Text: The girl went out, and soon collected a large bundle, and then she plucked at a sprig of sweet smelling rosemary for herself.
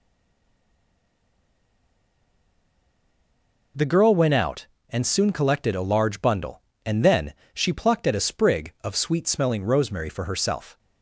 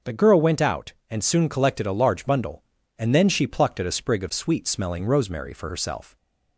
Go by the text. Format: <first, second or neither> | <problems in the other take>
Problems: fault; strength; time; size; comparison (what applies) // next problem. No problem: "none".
second | stays silent before the first word; strong; until 3.7 s; 3.7 s long // pauses between "then" and "she"; slight; at 7.3 s; 0.22 s long